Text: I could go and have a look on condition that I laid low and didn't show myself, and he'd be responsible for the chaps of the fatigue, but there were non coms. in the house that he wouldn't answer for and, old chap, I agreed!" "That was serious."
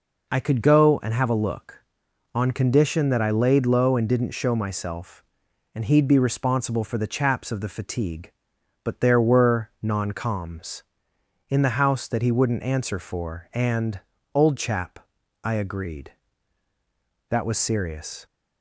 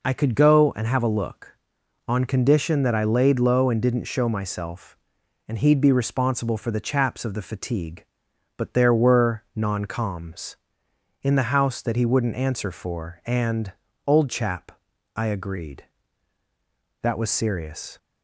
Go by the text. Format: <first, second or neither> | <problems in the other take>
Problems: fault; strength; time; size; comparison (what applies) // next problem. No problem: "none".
neither | none